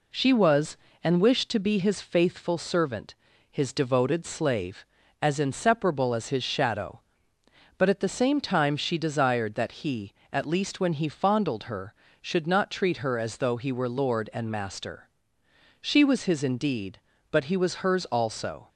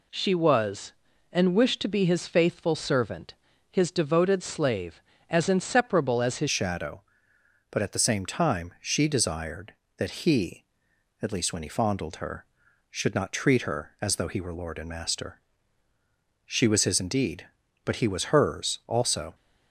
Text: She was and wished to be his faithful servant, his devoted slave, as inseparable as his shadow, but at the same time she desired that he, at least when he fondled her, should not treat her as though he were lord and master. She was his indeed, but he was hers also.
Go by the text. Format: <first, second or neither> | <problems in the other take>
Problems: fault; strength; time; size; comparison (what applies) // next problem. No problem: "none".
first | changes voice at "shadow"; from 6.5 s on; 12.8 s long